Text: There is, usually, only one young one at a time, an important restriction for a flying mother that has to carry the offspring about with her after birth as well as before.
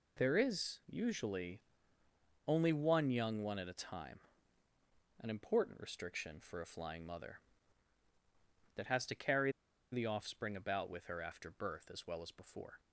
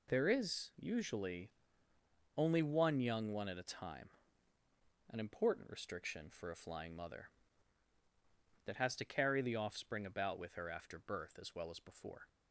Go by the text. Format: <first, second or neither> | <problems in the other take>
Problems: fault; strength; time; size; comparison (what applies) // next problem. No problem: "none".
second | pauses between "carry" and "the"; at 9.5 s; 0.40 s long